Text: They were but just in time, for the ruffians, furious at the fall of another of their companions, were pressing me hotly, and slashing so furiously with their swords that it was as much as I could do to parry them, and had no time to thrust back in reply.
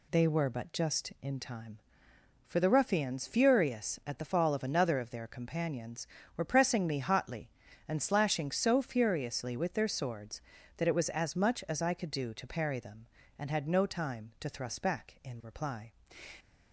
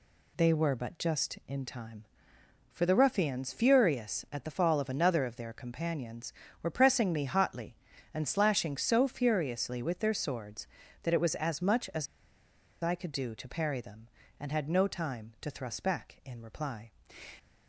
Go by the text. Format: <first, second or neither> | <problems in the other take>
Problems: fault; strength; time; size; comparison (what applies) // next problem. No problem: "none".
first | pauses between "as" and "I"; noticeable; at 12.0 s; 0.75 s long